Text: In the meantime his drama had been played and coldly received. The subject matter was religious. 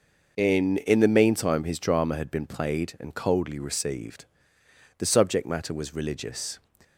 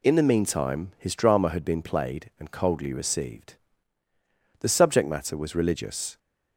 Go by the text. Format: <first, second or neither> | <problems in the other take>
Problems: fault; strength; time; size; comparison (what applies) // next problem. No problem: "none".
second | says "In" twice; at 0.7 s